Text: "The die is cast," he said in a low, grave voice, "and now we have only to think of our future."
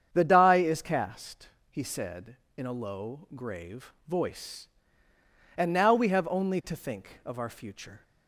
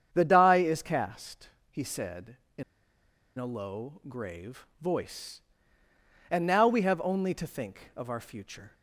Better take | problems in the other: first | starts louder than the rest; strong; until 1.1 s; 8 dB; strong in the first // pauses between "in" and "a"; noticeable; at 2.6 s; 0.75 s long // pauses between "grave" and "voice"; slight; at 4.6 s; 0.16 s long; slight in the first

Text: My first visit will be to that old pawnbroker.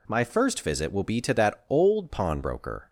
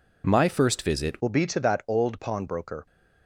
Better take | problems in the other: first | changes voice at "will"; from 1.2 s on; 1.6 s long

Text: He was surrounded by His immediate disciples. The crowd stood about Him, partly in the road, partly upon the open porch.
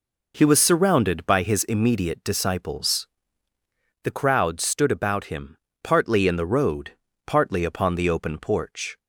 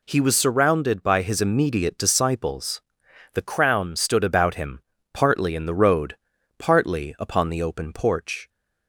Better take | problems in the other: first | says "crown" for "crowd"; at 3.4 s

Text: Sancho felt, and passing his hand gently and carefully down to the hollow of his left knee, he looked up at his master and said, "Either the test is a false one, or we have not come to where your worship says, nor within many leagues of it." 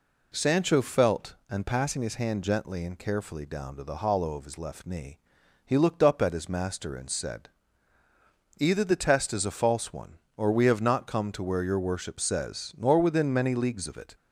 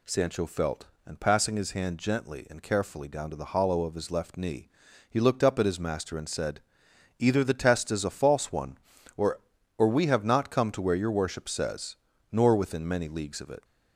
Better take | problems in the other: first | says "or" twice; at 9.7 s

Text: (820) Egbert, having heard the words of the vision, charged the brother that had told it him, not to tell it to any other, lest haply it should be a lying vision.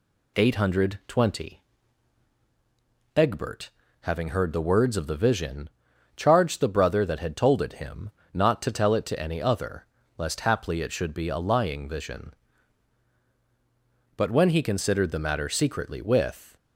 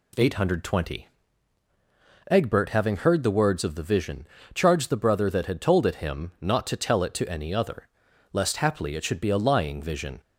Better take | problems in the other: second | goes on to say "But when he considered the matter secretly with"; strong; from 14.1 s on; 2.4 s long

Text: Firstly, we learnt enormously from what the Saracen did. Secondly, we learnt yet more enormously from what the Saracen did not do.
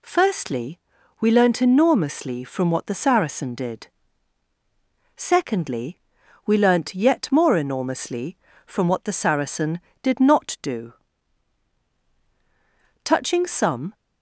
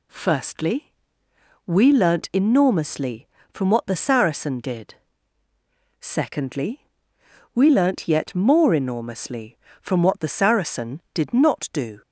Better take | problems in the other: second | goes on to say "Touching some"; noticeable; from 13.0 s on; 0.90 s long

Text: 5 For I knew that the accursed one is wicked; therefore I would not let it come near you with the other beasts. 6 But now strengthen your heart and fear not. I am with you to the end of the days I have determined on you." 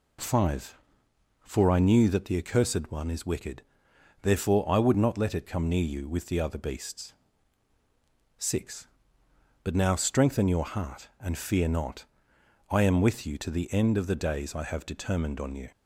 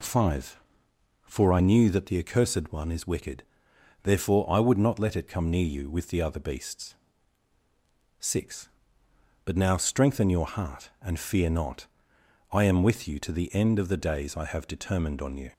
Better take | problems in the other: neither | none

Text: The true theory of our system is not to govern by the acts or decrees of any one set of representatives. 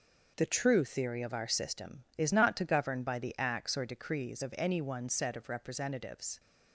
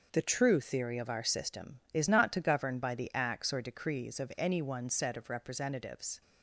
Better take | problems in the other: neither | none

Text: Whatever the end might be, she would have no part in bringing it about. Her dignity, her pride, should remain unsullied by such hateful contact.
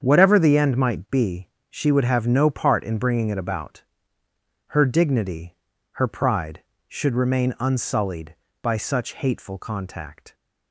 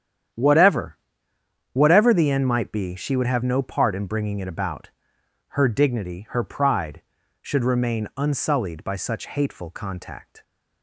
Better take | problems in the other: first | starts louder than the rest; strong; until 2.1 s; 9.5 dB; strong in the first // says "Whatever" twice; at 1.7 s

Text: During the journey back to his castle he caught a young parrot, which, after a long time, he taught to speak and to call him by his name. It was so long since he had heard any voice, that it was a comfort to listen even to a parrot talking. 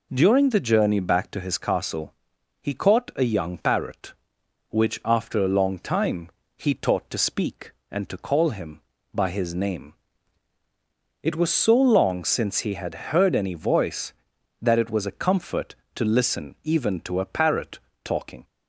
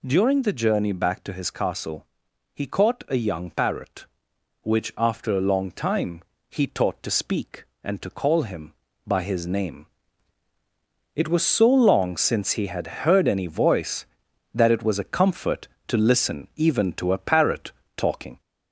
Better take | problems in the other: first | gets louder; slight; throughout; 2.5 dB // pauses between "castle" and "he"; noticeable; at 2.0 s; 0.48 s long; noticeable in the first // pauses between "parrot" and "talking"; slight; at 17.7 s; 0.26 s long; slight in the first

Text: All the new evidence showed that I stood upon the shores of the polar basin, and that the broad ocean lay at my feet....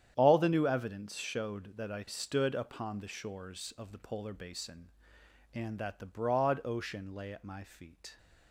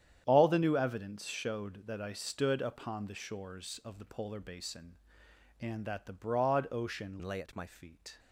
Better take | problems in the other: first | starts louder than the rest; strong; until 1.2 s; 9.5 dB; strong in the first // changes voice from "lay" to "my"; from 7.2 to 7.6 s; 0.4 s long

